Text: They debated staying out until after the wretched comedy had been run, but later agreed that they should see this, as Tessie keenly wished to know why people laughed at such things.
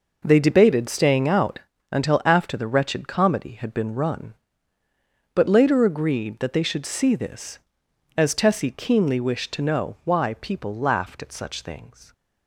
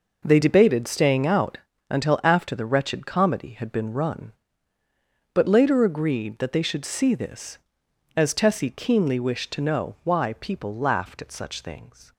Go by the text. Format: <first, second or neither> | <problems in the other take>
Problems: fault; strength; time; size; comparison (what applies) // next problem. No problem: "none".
neither | pauses between "out" and "until"; slight; the same in both